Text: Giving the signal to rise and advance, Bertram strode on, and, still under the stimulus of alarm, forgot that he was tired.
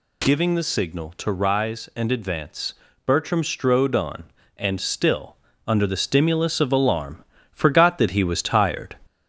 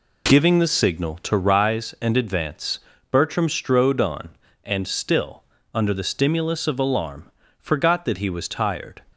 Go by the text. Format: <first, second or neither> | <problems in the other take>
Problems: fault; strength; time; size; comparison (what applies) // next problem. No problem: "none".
second | gets louder; slight; throughout; 2 dB // pauses between "still" and "under"; slight; at 5.3 s; 0.28 s long; slight in the second